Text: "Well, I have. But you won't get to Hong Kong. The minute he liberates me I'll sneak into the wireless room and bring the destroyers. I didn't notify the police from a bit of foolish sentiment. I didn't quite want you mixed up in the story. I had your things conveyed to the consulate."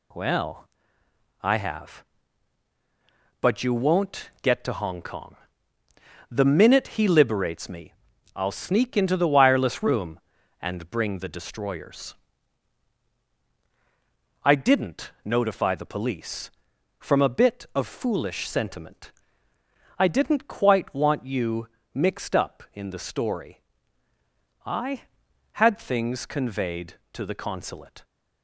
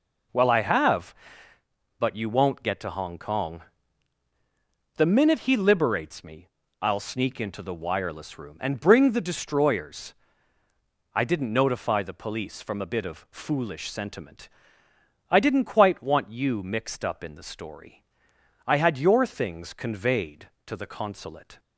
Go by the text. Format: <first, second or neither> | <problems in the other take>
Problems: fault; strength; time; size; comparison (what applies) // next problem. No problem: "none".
second | pauses between "me" and "I'll"; at 7.9 s; 0.40 s long; slight in the second // pauses between "you" and "mixed"; slight; at 21.6 s; 0.26 s long // skips "your"; at 25.7 s